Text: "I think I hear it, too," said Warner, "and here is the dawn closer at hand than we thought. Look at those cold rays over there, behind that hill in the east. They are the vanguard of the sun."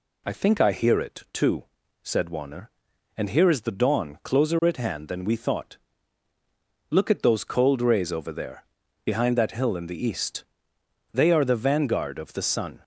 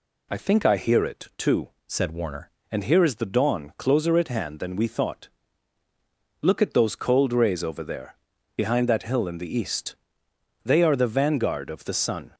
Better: first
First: none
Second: changes voice from "said" to "Warner"; from 1.8 to 2.4 s; 0.6 s long

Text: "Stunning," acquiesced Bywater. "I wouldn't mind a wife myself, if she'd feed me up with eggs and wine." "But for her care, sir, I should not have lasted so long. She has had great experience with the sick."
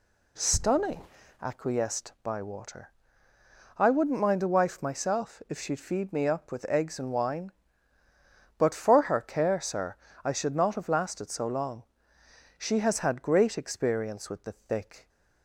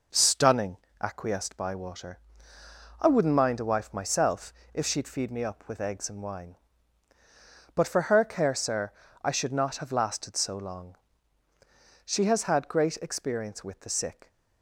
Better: second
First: says "thick" for "sick"; at 14.5 s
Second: none

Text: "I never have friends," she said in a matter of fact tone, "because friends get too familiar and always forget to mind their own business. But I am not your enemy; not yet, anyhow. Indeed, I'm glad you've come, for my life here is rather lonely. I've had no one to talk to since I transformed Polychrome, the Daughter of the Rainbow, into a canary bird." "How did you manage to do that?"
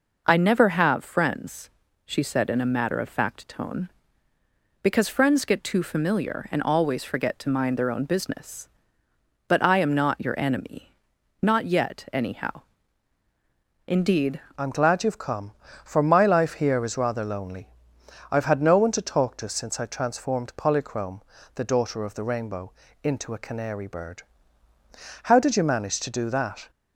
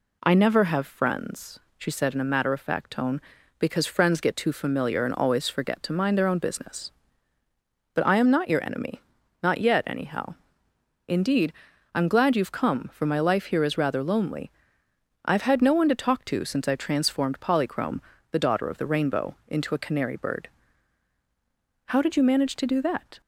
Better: second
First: changes voice at "I'm"; from 14.5 s on; 12.1 s long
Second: none

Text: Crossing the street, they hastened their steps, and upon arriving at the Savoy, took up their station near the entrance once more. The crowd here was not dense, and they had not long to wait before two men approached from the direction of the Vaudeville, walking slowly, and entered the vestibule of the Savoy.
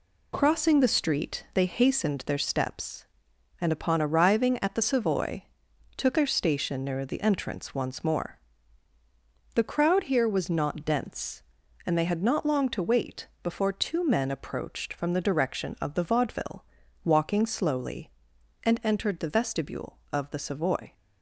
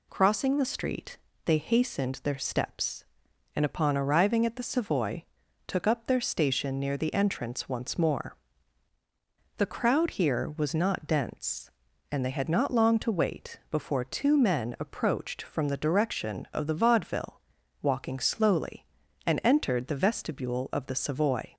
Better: second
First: skips "up"; at 6.1 s // pauses between "wait" and "before"; slight; at 13.2 s; 0.16 s long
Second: none

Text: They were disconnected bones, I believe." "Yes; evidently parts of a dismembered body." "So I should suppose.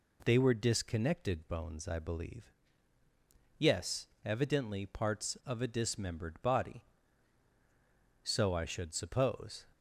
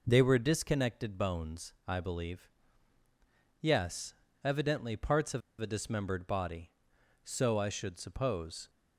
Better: first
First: none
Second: pauses between "of" and "a"; slight; at 5.4 s; 0.20 s long

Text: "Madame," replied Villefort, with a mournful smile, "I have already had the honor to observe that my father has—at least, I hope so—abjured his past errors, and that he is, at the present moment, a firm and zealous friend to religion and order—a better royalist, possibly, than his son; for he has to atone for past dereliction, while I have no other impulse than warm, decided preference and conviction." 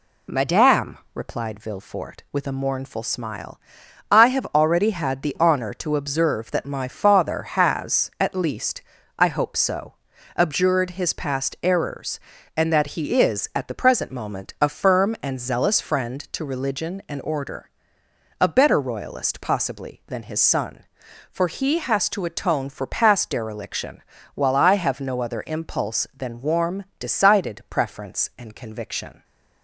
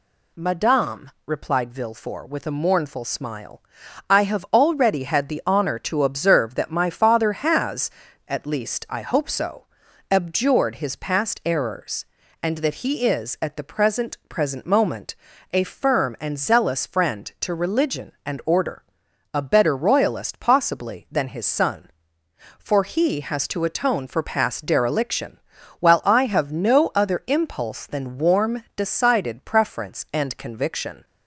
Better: first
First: none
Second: says "present" twice; at 14.2 s

